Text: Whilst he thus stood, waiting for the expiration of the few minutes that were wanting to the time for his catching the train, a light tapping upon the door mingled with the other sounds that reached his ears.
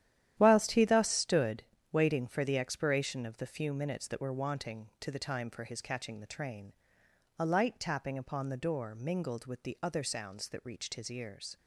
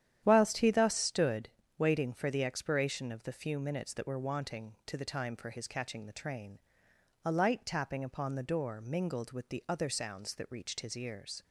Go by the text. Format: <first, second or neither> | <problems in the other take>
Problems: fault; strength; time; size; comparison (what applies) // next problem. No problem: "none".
second | gets quieter; strong; throughout; 11.5 dB // starts louder than the rest; strong; until 1.3 s; 11.5 dB; strong in the second